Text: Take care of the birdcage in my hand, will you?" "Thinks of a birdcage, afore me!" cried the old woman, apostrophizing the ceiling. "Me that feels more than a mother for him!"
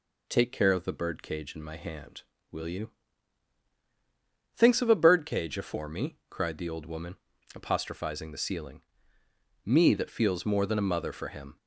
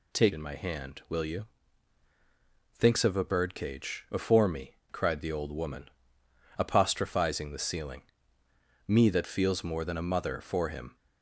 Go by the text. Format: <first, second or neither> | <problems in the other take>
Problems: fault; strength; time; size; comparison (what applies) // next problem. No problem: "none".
first | skips "care of the birdcage"; at 0.3 s